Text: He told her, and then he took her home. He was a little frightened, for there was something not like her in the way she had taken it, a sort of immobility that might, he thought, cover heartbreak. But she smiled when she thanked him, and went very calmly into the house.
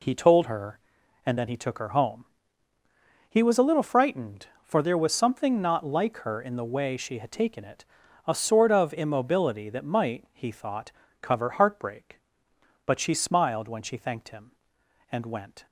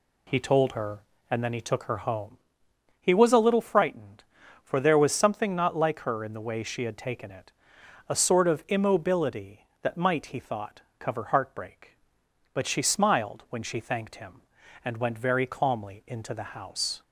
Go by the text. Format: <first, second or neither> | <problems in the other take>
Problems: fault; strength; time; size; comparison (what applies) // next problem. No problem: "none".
second | stops before "very calmly into the house"; at 15.6 s